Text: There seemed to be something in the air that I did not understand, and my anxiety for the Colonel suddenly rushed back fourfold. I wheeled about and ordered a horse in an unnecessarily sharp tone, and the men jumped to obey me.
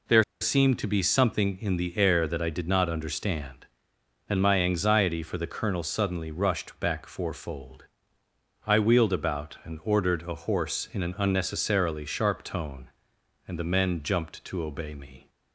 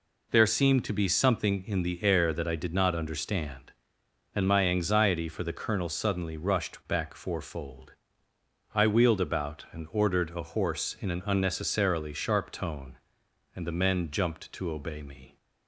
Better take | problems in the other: second | pauses between "There" and "seemed"; slight; at 0.2 s; 0.17 s long

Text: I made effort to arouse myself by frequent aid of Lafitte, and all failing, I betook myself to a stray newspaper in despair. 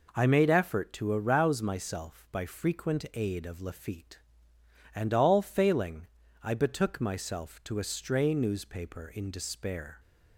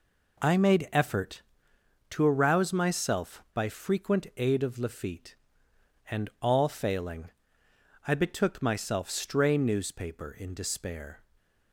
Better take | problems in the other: first | skips "to a"; at 9.1 s // stays silent after the last word; slight; from 11.2 s on; 0.5 s long

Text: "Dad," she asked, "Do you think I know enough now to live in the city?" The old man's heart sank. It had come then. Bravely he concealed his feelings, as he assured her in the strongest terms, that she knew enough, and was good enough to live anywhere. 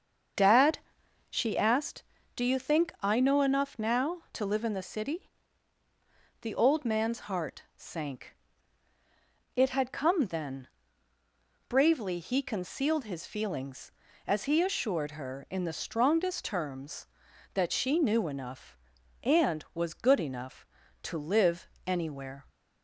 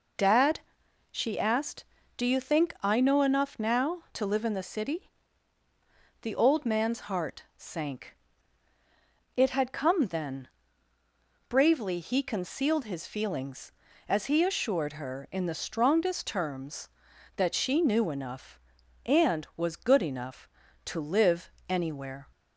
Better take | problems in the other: second | starts louder than the rest; until 1.9 s; 7 dB // pauses between "live" and "anywhere"; slight; at 21.6 s; 0.20 s long; slight in the second

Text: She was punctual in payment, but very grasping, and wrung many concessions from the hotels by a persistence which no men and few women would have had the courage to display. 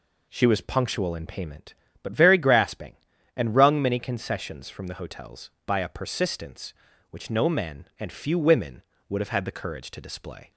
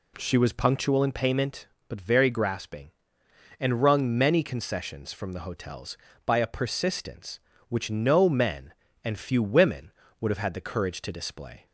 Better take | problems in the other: neither | none

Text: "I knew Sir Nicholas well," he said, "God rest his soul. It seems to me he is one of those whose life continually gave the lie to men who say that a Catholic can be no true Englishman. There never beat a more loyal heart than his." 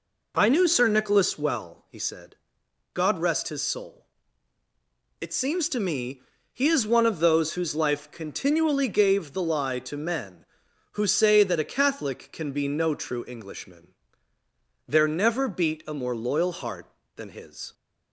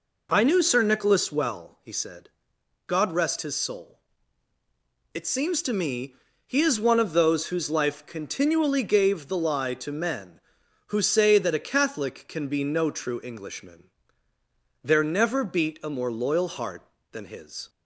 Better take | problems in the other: neither | pauses between "me" and "he"; slight; the same in both

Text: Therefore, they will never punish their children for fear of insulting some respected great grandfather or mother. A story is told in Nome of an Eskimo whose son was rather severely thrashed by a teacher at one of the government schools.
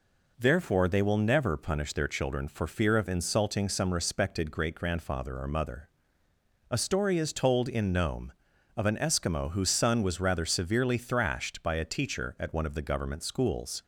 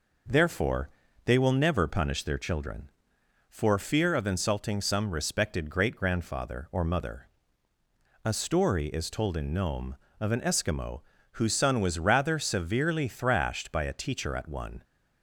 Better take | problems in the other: first | pauses between "Eskimo" and "whose"; slight; at 11.0 s; 0.32 s long // stops before "of the government schools"; at 14.8 s

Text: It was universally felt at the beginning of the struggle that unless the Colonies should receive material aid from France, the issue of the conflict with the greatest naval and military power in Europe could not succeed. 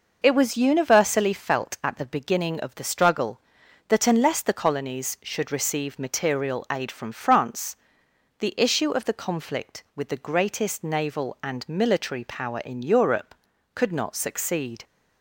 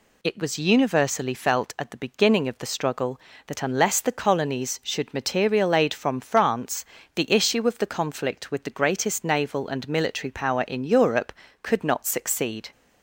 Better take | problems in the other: first | skips "receive"; at 5.1 s

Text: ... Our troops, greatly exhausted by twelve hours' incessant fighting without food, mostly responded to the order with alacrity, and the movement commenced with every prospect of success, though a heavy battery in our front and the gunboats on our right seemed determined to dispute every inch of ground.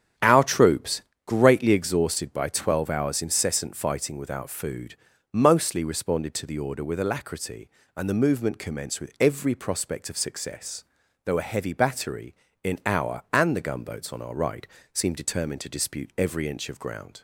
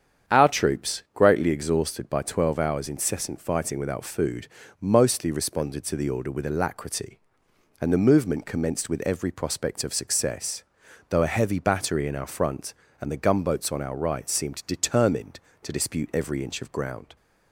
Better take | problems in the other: second | starts louder than the rest; strong; until 1.4 s; 8.5 dB; strong in the second // skips "front"; at 13.2 s // pauses between "right" and "seemed"; slight; at 14.6 s; 0.26 s long

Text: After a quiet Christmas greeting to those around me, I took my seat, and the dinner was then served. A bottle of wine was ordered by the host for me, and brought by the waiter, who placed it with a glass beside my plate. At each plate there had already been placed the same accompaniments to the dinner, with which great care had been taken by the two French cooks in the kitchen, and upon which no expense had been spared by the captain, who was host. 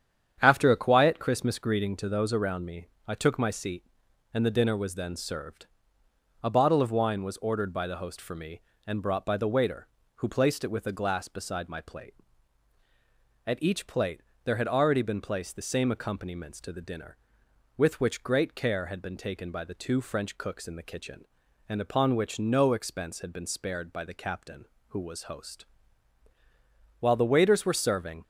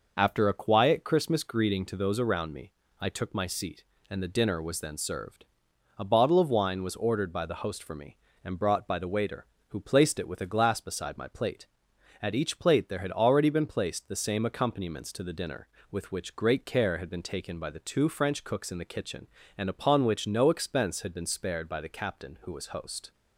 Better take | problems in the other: second | starts louder than the rest; strong; until 1.4 s; 8.5 dB // pauses between "plate" and "there"; slight; at 14.2 s; 0.24 s long // goes on to say "While the waiters were serving"; noticeable; from 27.0 s on; 1.2 s long

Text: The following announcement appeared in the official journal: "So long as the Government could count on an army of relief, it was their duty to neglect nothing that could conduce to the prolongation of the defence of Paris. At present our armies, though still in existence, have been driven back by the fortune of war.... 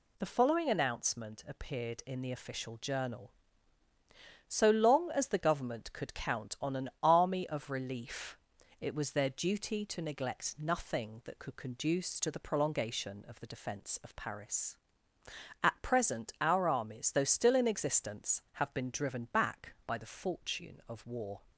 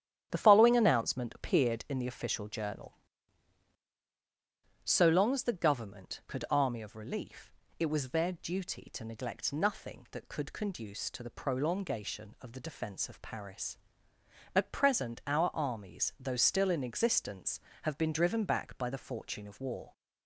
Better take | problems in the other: first | starts louder than the rest; strong; until 1.3 s; 10 dB // skips "count on an"; at 6.4 s

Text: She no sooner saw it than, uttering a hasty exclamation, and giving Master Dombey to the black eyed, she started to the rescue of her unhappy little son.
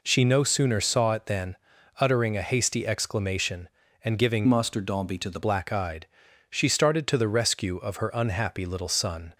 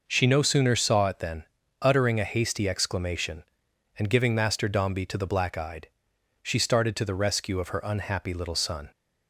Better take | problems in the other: second | changes voice from "Master" to "the"; from 4.4 to 5.3 s; 0.9 s long

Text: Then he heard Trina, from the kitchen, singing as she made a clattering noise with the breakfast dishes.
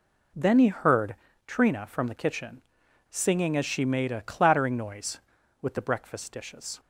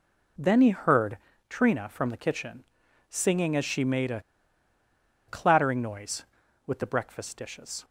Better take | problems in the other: first | pauses between "heard" and "Trina"; slight; at 1.1 s; 0.32 s long; slight in the first // pauses between "a" and "clattering"; at 4.2 s; 1.0 s long

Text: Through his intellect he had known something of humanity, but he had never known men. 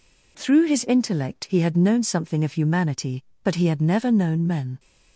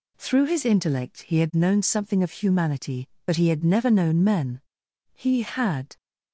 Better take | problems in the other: first | goes on to say "He had"; noticeable; from 5.1 s on; 0.84 s long

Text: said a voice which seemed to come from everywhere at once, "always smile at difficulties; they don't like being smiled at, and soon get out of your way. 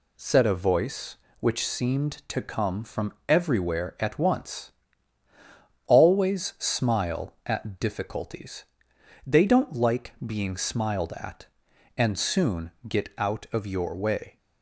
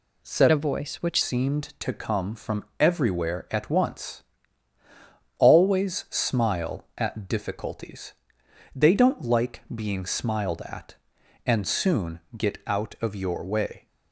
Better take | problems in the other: first | changes voice from "a" to "which"; from 0.5 to 1.2 s; 0.7 s long // pauses between "from" and "everywhere"; slight; at 2.6 s; 0.16 s long; slight in the first // pauses between "soon" and "get"; slight; at 12.1 s; 0.16 s long; slight in the first

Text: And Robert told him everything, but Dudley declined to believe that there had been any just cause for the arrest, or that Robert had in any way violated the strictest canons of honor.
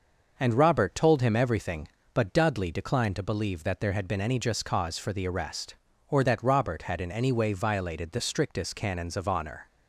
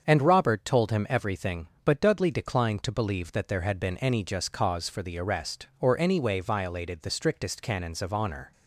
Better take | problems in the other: first | starts louder than the rest; until 1.1 s; 7 dB // skips "that Robert had in"; at 5.9 s

